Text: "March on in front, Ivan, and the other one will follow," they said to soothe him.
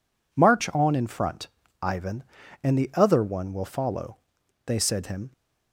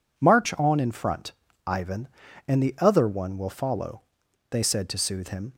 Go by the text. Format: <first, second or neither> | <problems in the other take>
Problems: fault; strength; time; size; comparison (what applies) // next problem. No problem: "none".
second | skips "to soothe"; at 5.0 s